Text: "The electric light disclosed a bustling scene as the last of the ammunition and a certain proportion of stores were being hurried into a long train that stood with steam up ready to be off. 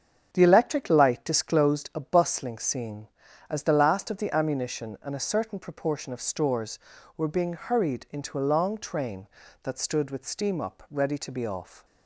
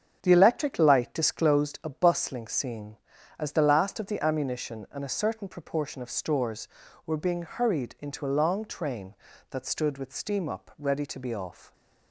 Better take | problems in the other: neither | starts louder than the rest; strong; the same in both

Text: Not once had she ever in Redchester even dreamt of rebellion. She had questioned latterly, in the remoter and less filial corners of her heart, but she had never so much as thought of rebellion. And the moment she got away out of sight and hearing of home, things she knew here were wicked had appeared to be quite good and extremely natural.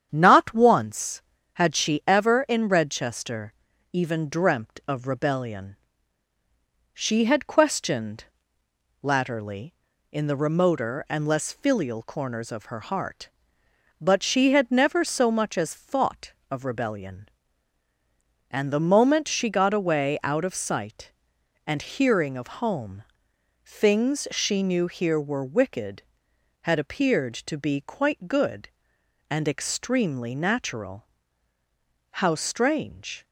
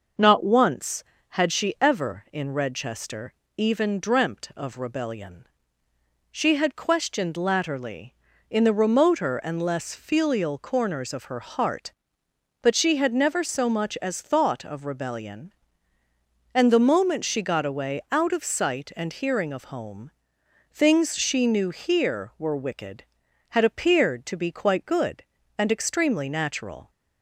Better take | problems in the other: second | starts louder than the rest; strong; until 1.1 s; 8.5 dB; noticeable in the second // pauses between "Redchester" and "even"; at 3.5 s; 0.40 s long; slight in the second // pauses between "questioned" and "latterly"; noticeable; at 8.2 s; 0.78 s long // goes on to say "How strange"; noticeable; from 32.1 s on; 1.1 s long

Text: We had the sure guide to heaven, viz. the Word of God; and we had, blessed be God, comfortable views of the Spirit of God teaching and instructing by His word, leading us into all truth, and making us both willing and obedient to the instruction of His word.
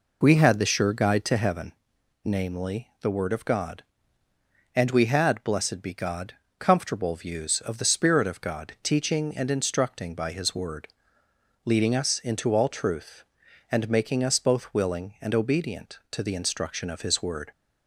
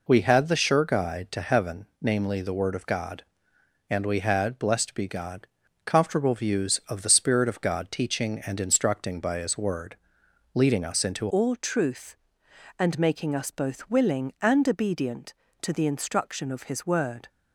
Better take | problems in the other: first | changes voice at "all"; from 11.2 s on; 6.0 s long

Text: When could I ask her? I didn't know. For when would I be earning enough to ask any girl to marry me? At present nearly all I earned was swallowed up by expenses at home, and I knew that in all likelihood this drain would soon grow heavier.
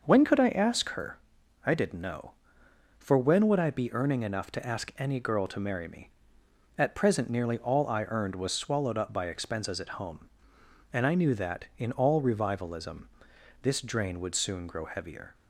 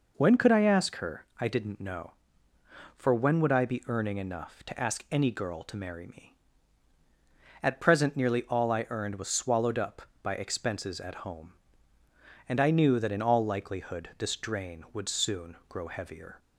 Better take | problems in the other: second | starts louder than the rest; noticeable; until 1.0 s; 6 dB // says "revivalism" for "likelihood"; at 12.2 s

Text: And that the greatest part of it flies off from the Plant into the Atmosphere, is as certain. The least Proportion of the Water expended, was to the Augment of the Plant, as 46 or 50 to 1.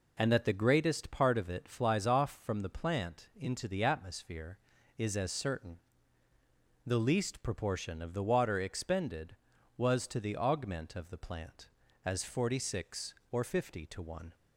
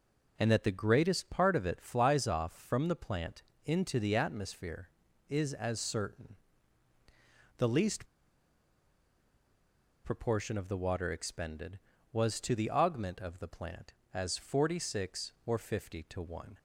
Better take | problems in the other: first | pauses between "Plant" and "into"; slight; at 3.4 s; 0.24 s long // pauses between "least" and "Proportion"; strong; at 8.0 s; 1.9 s long

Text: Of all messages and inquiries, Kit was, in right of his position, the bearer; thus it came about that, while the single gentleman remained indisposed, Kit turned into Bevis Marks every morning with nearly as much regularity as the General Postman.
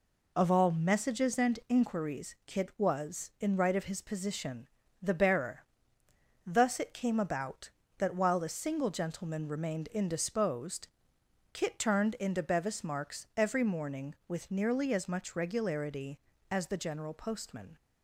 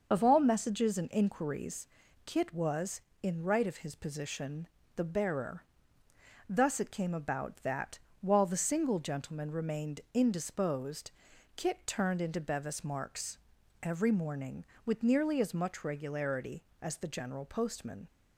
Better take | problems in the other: first | loses the start of "Of"; at 0.1 s; 55 ms // starts louder than the rest; noticeable; until 1.1 s; 6 dB // pauses between "Marks" and "every"; at 13.3 s; 0.44 s long

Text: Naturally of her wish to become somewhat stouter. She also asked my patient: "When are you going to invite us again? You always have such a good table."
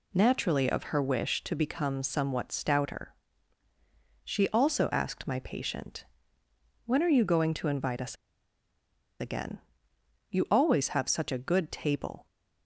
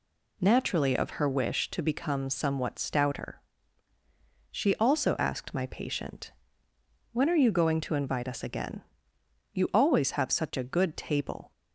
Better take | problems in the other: second | pauses between "us" and "again"; at 8.1 s; 1.0 s long

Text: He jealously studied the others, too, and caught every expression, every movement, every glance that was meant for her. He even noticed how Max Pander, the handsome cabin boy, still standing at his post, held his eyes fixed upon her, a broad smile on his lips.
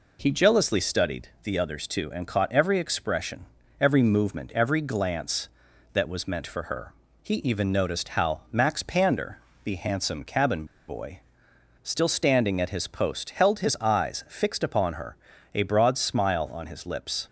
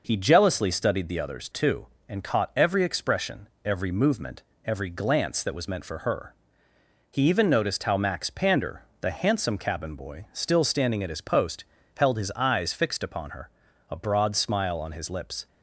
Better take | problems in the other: second | pauses between "studied" and "the"; slight; at 1.2 s; 0.16 s long // pauses between "cabin" and "boy"; slight; at 10.6 s; 0.23 s long

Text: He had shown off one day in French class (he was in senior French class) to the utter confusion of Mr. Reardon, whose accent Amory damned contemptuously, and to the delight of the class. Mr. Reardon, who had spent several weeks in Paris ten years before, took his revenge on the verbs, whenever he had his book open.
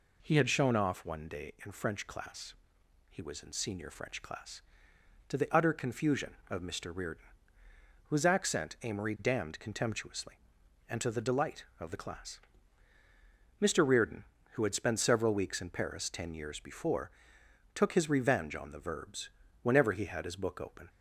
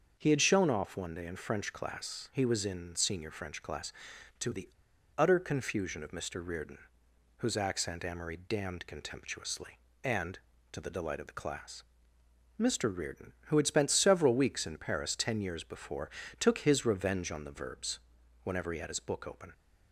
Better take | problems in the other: first | starts louder than the rest; until 1.2 s; 6.5 dB // pauses between "the" and "utter"; noticeable; at 4.6 s; 0.50 s long

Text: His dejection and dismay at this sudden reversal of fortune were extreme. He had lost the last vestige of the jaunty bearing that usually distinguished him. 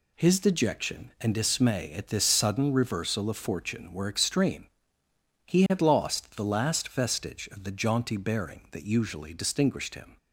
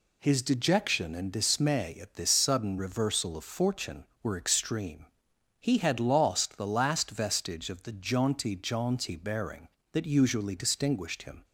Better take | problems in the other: first | says "jaunty" twice; at 8.5 s

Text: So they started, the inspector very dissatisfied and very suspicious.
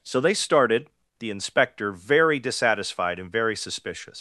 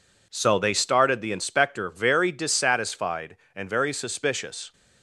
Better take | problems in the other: second | leaves "suspicious" unfinished; at 4.1 s; 140 ms

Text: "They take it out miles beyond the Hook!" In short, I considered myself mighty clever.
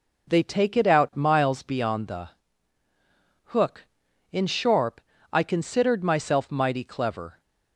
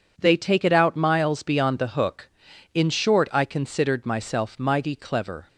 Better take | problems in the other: second | pauses between "the" and "Hook"; at 2.2 s; 1.1 s long // says "sharp" for "short"; at 4.4 s

